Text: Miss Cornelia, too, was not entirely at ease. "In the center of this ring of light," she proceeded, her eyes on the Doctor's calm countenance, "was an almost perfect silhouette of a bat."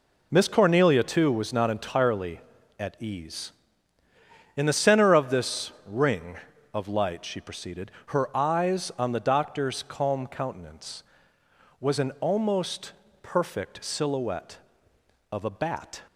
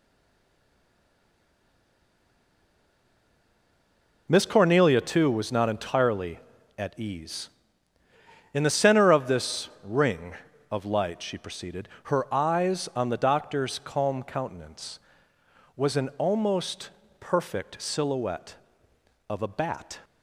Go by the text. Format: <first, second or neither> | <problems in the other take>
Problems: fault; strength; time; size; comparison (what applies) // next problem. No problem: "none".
first | stays silent before the first word; strong; until 4.2 s; 4.2 s long // pauses between "this" and "ring"; slight; at 9.6 s; 0.16 s long; slight in the first // pauses between "almost" and "perfect"; slight; at 16.8 s; 0.30 s long; slight in the first